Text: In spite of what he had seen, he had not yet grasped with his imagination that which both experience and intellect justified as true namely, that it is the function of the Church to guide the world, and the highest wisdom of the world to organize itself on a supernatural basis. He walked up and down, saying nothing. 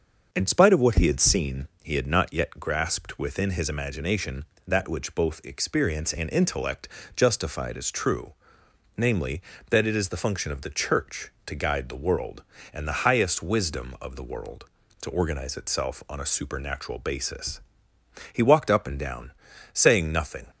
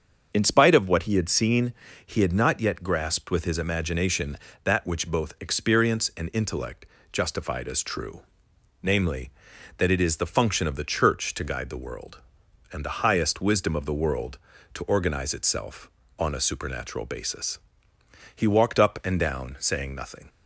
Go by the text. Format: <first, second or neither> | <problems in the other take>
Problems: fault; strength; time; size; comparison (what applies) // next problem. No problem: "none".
second | starts louder than the rest; until 1.3 s; 6.5 dB; also in the second // says "within" for "with"; at 3.1 s // pauses between "intellect" and "justified"; slight; at 6.8 s; 0.30 s long; slight in the second // pauses between "true" and "namely"; noticeable; at 8.3 s; 0.64 s long; noticeable in the second